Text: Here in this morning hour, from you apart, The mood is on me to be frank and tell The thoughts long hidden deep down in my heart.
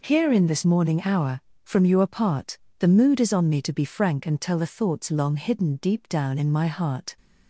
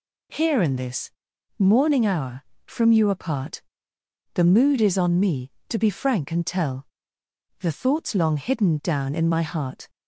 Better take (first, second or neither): first